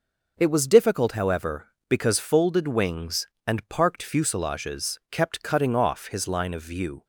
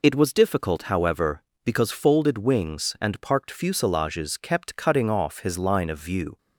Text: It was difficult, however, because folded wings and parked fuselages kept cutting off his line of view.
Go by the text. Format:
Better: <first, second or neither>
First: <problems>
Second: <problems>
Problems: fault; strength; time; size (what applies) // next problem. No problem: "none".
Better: neither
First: none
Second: none